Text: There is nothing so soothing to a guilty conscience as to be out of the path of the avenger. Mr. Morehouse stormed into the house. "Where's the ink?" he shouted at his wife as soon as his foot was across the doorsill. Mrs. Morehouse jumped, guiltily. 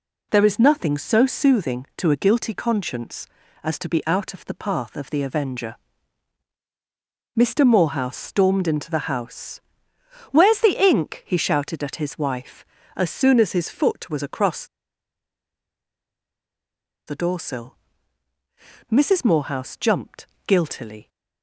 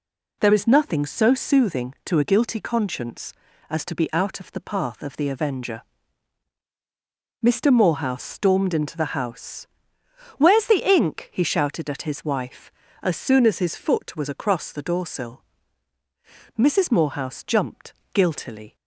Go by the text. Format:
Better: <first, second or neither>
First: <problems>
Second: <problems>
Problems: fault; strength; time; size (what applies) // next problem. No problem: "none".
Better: second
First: pauses between "across" and "the"; strong; at 14.6 s; 2.4 s long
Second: none